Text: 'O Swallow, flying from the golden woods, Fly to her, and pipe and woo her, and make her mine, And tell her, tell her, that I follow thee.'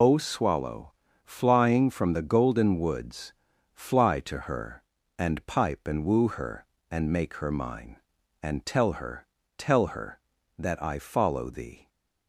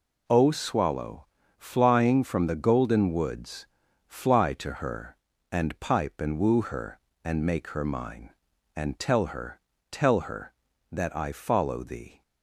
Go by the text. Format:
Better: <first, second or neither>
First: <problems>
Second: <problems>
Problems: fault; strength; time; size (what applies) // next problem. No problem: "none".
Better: second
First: loses the start of "O"; at 0.0 s; 60 ms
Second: none